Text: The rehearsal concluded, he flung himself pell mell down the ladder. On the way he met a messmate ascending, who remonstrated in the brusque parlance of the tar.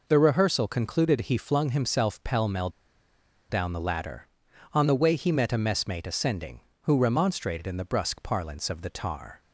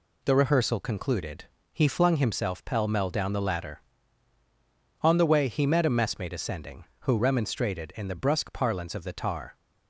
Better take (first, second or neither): second